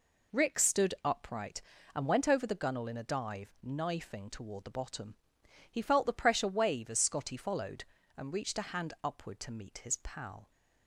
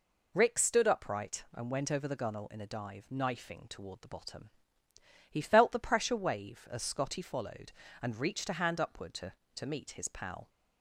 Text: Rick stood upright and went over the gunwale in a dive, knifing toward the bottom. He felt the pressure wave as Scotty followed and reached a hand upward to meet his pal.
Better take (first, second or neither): first